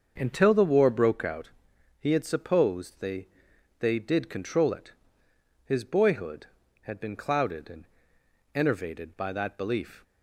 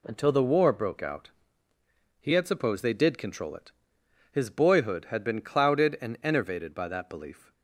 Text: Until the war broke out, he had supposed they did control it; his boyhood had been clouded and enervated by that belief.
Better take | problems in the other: second | starts louder than the rest; until 1.1 s; 6.5 dB // says "they" twice; at 3.8 s // pauses between "and" and "enervated"; noticeable; at 7.8 s; 0.70 s long

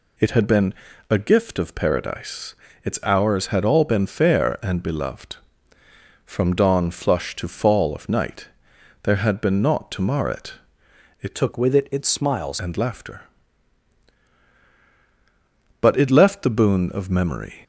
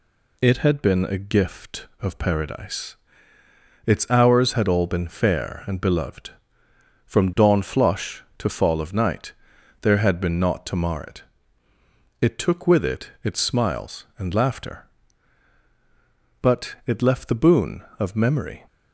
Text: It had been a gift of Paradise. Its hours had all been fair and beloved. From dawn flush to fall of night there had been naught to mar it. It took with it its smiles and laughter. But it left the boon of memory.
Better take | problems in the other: second | pauses between "been" and "a"; at 0.7 s; 0.38 s long // pauses between "night" and "there"; noticeable; at 8.4 s; 0.54 s long; noticeable in the second // changes voice from "took" to "smiles"; from 11.3 to 12.5 s; 1.2 s long

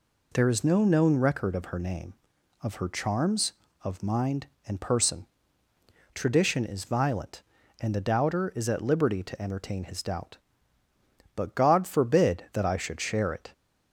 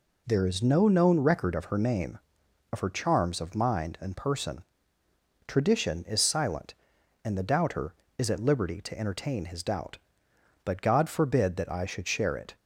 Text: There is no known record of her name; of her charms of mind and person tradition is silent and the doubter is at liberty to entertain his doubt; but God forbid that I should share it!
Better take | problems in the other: second | pauses between "person" and "tradition"; noticeable; at 5.2 s; 0.88 s long; noticeable in the second // says "violent" for "silent"; at 6.8 s

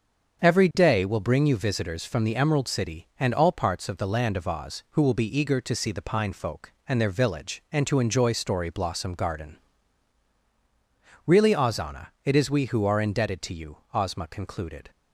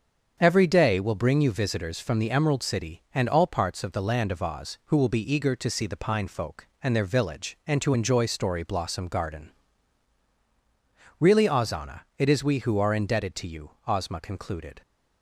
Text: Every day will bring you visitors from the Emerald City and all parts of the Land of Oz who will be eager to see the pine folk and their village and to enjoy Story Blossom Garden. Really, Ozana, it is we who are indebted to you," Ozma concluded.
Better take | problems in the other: neither | starts louder than the rest; the same in both

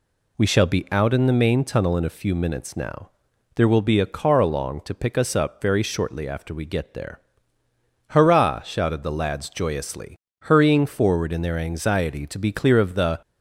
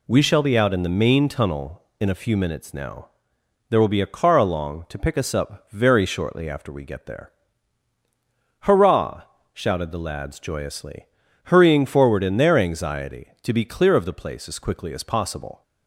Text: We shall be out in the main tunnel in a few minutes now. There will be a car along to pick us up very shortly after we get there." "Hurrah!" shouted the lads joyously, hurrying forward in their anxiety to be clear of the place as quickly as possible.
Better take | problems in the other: second | stops before "place as quickly as possible"; at 13.2 s

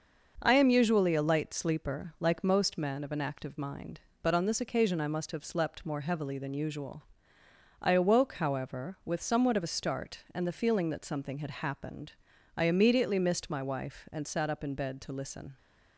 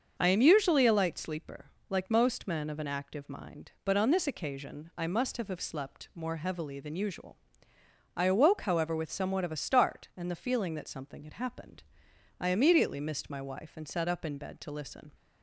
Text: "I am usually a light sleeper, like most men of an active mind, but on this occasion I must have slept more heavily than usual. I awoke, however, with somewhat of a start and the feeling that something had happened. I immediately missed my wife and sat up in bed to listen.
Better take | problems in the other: first | starts louder than the rest; until 1.1 s; 6.5 dB // says "have" twice; at 5.4 s

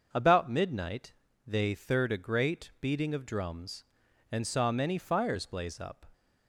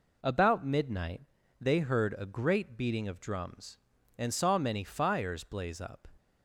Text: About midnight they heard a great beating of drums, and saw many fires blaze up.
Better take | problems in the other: second | starts louder than the rest; until 1.1 s; 6.5 dB // pauses between "midnight" and "they"; slight; at 1.1 s; 0.34 s long; also in the second // says "third" for "heard"; at 1.7 s

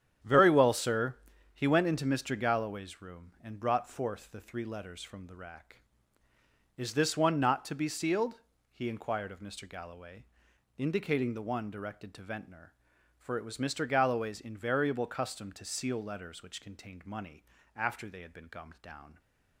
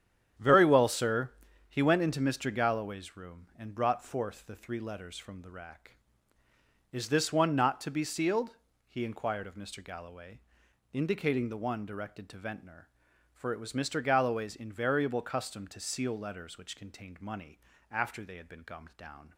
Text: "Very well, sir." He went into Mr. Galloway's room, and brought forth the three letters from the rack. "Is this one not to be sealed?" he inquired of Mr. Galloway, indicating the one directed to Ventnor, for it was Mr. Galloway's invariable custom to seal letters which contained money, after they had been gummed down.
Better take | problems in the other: neither | starts louder than the rest; strong; the same in both

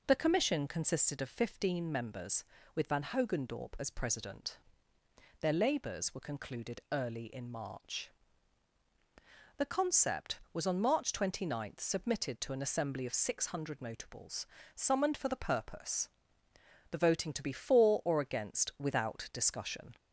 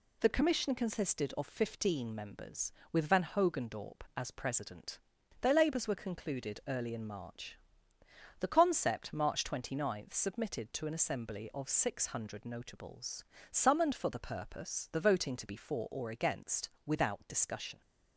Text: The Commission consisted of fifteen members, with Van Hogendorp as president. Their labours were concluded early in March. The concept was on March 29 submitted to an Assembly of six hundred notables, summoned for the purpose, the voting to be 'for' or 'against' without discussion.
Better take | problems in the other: first | skips "was on"; at 9.1 s // pauses between "against" and "without"; slight; at 16.7 s; 0.16 s long

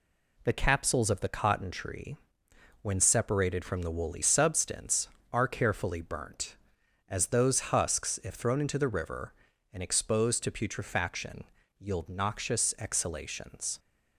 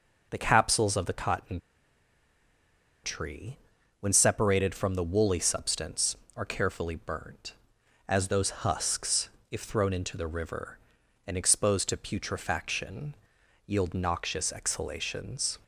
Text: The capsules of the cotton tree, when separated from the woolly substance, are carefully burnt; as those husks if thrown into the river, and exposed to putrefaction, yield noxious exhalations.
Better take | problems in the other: first | pauses between "cotton" and "tree"; strong; at 1.5 s; 1.4 s long // pauses between "husks" and "if"; slight; at 9.2 s; 0.20 s long

